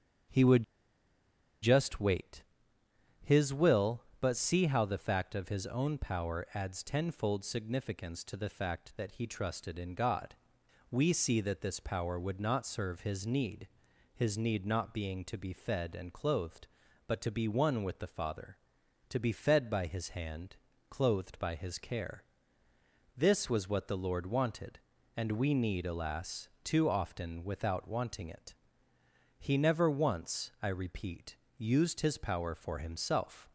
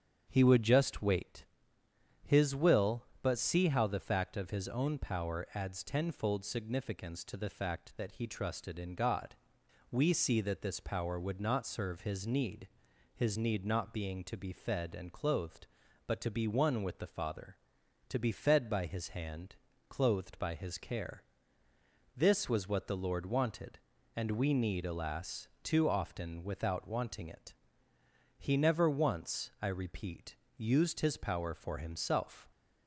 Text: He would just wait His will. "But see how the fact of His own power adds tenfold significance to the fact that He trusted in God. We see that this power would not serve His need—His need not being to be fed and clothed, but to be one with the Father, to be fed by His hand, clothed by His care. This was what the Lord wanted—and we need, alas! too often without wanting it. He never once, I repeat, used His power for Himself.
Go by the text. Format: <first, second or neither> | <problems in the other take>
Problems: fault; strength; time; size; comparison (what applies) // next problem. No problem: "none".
second | starts louder than the rest; strong; until 2.2 s; 8 dB; strong in the second // pauses between "would" and "just"; at 0.6 s; 0.98 s long // pauses between "wait" and "His"; noticeable; at 2.4 s; 0.78 s long; noticeable in the second